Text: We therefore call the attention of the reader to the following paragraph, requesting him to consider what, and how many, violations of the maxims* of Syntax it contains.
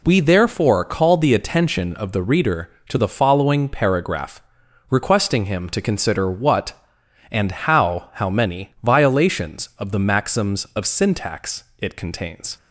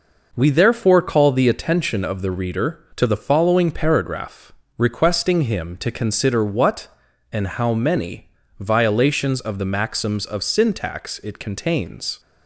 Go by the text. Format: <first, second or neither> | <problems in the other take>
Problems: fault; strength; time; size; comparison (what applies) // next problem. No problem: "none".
second | says "how" twice; at 8.1 s // pauses between "Syntax" and "it"; slight; at 11.6 s; 0.16 s long